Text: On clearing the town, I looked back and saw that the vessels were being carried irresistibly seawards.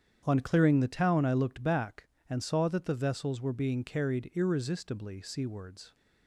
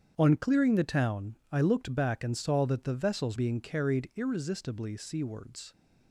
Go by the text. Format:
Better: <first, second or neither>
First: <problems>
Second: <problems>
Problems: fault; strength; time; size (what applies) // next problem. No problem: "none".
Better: first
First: starts louder than the rest; strong; until 1.2 s; 8.5 dB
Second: starts louder than the rest; strong; until 1.1 s; 8 dB // skips "were"; at 3.3 s